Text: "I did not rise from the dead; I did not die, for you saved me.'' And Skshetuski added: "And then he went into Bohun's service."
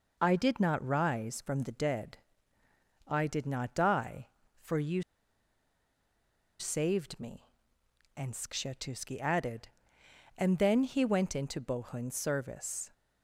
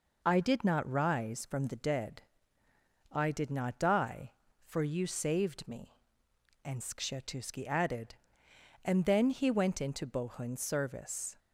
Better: second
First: pauses between "you" and "saved"; strong; at 5.0 s; 1.5 s long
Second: none

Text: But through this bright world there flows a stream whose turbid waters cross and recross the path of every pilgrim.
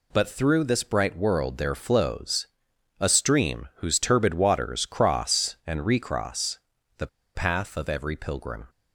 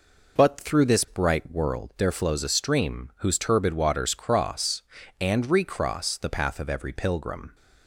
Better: second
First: pauses between "flows" and "a"; noticeable; at 2.4 s; 0.52 s long // pauses between "recross" and "the"; at 6.5 s; 0.38 s long // pauses between "the" and "path"; slight; at 7.0 s; 0.27 s long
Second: none

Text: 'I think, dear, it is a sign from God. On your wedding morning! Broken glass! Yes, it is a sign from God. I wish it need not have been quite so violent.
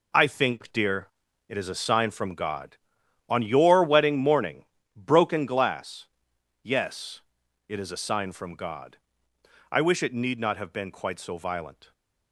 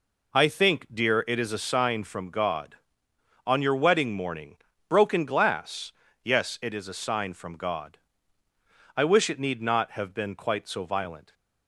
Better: neither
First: none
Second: none

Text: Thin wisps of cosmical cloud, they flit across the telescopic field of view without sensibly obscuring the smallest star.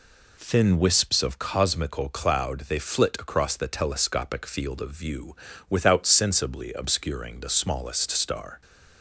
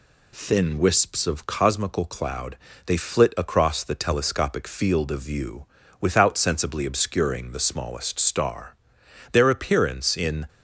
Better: first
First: pauses between "view" and "without"; slight; at 5.3 s; 0.32 s long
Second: pauses between "view" and "without"; slight; at 5.6 s; 0.34 s long // goes on to say "Their appearance in"; noticeable; from 9.3 s on; 1.1 s long

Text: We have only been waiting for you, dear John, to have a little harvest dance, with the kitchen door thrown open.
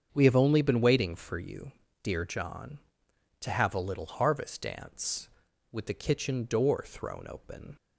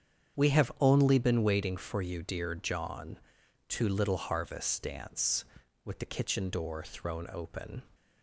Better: first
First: starts louder than the rest; strong; until 1.1 s; 7 dB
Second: starts louder than the rest; strong; until 1.4 s; 8 dB // skips "have a"; at 3.8 s

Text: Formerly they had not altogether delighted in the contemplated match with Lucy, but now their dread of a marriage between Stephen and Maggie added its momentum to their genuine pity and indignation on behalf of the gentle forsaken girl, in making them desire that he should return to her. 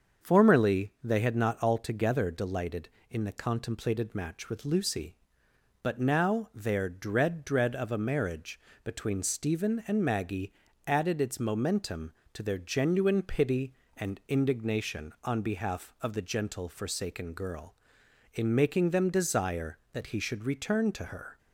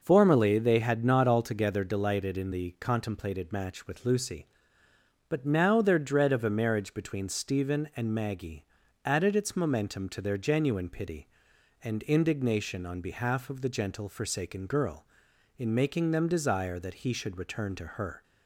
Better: second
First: starts louder than the rest; until 1.3 s; 6.5 dB // says "dread" twice; at 7.4 s // pauses between "marriage" and "between"; slight; at 8.6 s; 0.24 s long // pauses between "Maggie" and "added"; slight; at 10.5 s; 0.34 s long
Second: pauses between "Maggie" and "added"; at 8.6 s; 0.40 s long

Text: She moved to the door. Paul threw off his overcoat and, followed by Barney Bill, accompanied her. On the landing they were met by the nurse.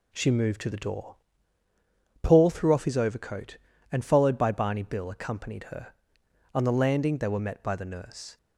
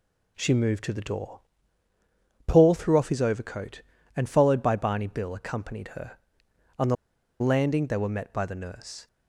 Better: first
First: none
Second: pauses between "the" and "landing"; at 6.9 s; 0.45 s long

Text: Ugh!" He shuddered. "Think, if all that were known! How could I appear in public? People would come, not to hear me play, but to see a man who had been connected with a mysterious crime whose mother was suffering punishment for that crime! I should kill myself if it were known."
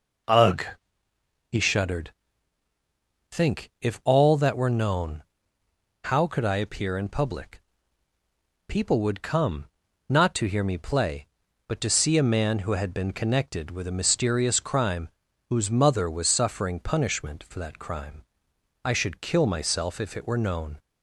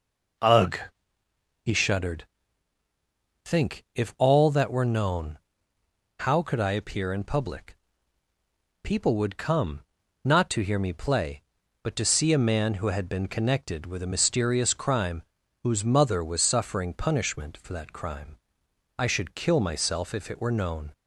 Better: neither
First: pauses between "crime" and "whose"; at 15.0 s; 0.40 s long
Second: pauses between "crime" and "whose"; at 15.2 s; 0.40 s long

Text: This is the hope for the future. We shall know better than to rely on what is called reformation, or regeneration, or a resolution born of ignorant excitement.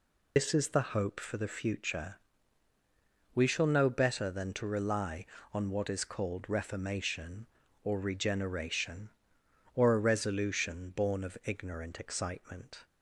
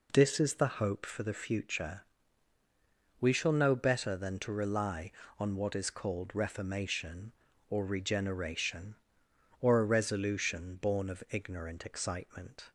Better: second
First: loses the start of "This"; at 0.3 s; 120 ms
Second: none

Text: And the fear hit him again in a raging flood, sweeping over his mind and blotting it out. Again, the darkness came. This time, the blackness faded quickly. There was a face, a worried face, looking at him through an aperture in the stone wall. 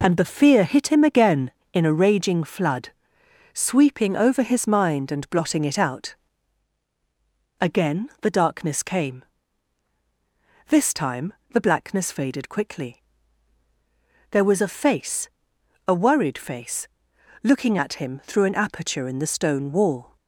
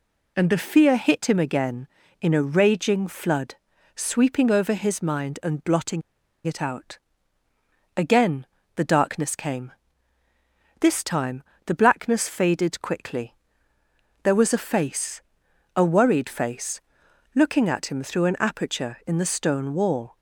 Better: first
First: none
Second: pauses between "blotting" and "it"; at 6.0 s; 0.44 s long

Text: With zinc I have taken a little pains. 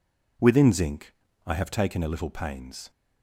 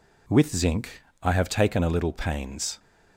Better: second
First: says "Within" for "With"; at 0.3 s // pauses between "zinc" and "I"; slight; at 1.1 s; 0.32 s long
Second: pauses between "zinc" and "I"; slight; at 0.8 s; 0.34 s long

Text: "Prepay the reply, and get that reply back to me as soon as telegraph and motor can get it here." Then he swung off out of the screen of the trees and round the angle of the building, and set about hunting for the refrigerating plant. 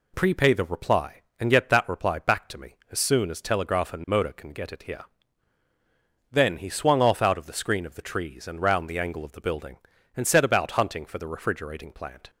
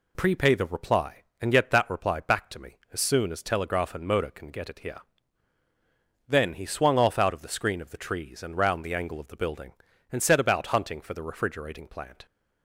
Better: neither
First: none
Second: none

